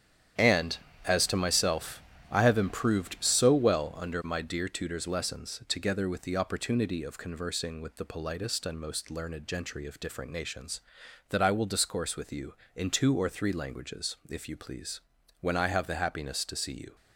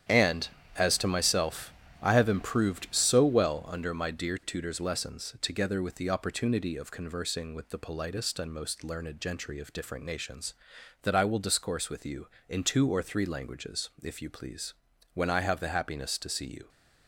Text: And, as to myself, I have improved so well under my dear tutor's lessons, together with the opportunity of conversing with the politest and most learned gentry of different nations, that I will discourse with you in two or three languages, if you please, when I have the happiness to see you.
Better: neither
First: starts louder than the rest; strong; until 1.6 s; 9.5 dB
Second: starts louder than the rest; strong; until 1.3 s; 9.5 dB

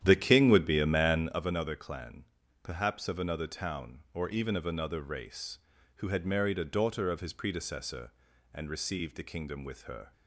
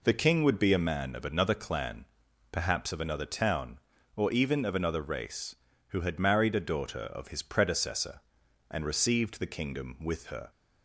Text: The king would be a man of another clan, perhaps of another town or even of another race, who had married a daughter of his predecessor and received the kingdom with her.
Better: second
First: starts louder than the rest; strong; until 1.5 s; 10.5 dB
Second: none

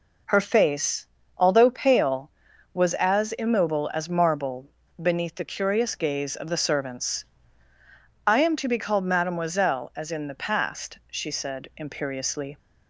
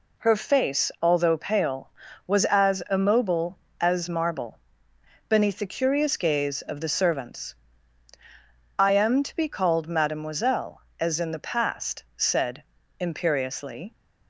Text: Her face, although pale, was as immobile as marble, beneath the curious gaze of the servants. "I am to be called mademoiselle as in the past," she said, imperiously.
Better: first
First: none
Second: skips "she"; at 12.0 s

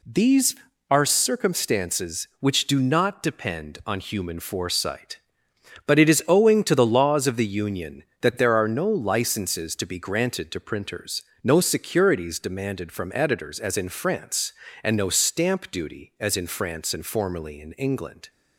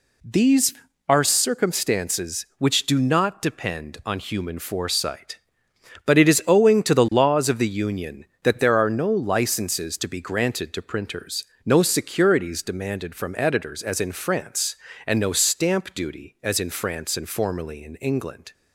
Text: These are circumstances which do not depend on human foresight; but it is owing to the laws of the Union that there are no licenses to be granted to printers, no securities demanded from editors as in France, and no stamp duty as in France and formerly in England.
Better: neither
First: none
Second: none

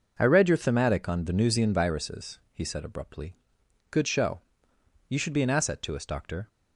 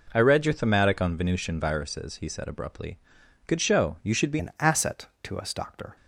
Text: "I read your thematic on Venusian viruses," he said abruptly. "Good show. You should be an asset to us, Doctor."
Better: first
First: none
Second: changes voice at "an"; from 4.3 s on; 1.6 s long

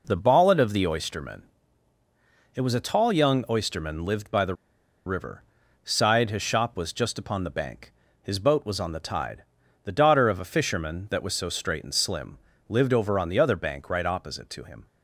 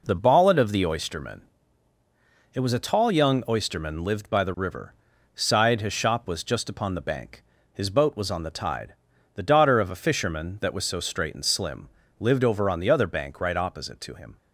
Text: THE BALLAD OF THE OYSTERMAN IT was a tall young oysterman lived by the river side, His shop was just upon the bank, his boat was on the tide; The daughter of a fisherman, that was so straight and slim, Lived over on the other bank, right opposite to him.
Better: second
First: pauses between "OYSTERMAN" and "IT"; at 1.4 s; 1.1 s long // pauses between "the" and "river"; noticeable; at 4.5 s; 0.52 s long // pauses between "river" and "side"; at 5.4 s; 0.42 s long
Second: pauses between "OYSTERMAN" and "IT"; at 1.4 s; 1.1 s long // pauses between "river" and "side"; at 4.9 s; 0.42 s long

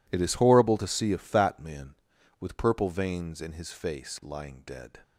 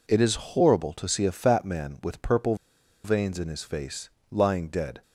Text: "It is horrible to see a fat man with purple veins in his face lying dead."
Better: first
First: none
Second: pauses between "purple" and "veins"; noticeable; at 2.5 s; 0.49 s long // pauses between "face" and "lying"; slight; at 4.0 s; 0.20 s long

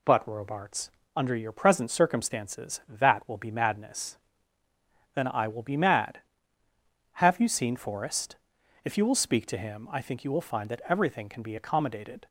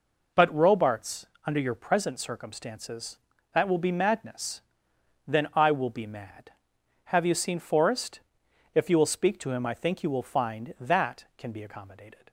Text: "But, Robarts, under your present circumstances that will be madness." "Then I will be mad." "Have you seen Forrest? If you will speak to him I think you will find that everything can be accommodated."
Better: first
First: none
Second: skips "everything"; at 11.3 s

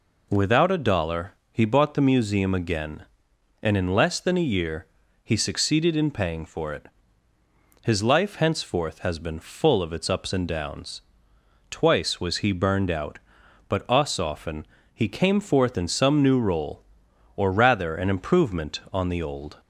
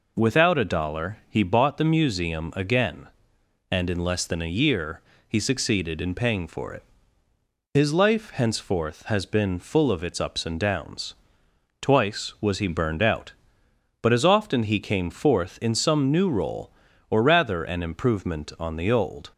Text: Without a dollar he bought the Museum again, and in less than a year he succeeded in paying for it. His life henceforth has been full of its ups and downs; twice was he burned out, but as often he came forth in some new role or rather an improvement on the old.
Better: second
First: pauses between "dollar" and "he"; slight; at 1.3 s; 0.20 s long // pauses between "year" and "he"; at 4.8 s; 0.38 s long // says "us" for "as"; at 13.8 s // pauses between "often" and "he"; slight; at 14.6 s; 0.28 s long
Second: pauses between "year" and "he"; slight; at 5.0 s; 0.26 s long

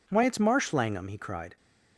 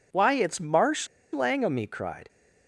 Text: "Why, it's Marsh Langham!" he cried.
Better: first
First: none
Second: pauses between "Marsh" and "Langham"; slight; at 1.0 s; 0.26 s long

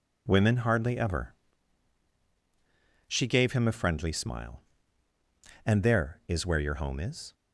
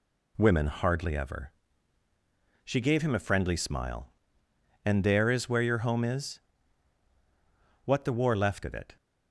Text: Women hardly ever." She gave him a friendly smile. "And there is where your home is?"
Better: first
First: none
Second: goes on to say "What the war left of it"; noticeable; from 7.8 s on; 1.1 s long

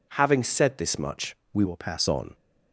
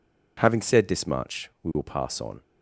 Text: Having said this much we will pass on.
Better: second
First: pauses between "much" and "we"; slight; at 1.3 s; 0.16 s long // changes voice from "will" to "pass"; from 1.6 to 2.0 s; 0.4 s long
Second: none

